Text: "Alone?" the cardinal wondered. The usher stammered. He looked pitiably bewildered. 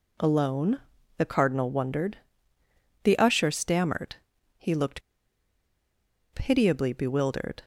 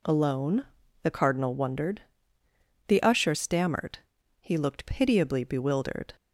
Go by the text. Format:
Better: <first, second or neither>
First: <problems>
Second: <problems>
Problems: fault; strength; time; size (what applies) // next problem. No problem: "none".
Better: second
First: pauses between "looked" and "pitiably"; strong; at 5.0 s; 1.3 s long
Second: none